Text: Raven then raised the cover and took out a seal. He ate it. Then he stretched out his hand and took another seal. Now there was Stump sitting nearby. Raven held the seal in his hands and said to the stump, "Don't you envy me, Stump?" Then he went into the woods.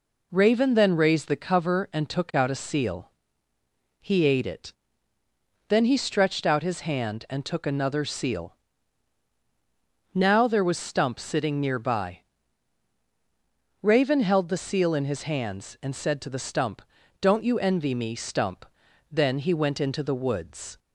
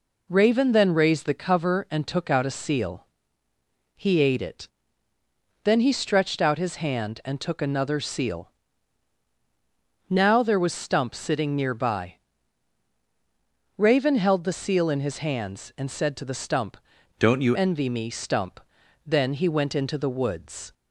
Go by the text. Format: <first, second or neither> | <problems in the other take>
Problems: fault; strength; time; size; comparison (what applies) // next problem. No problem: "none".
first | changes voice from "Don't" to "you"; from 17.1 to 17.5 s; 0.4 s long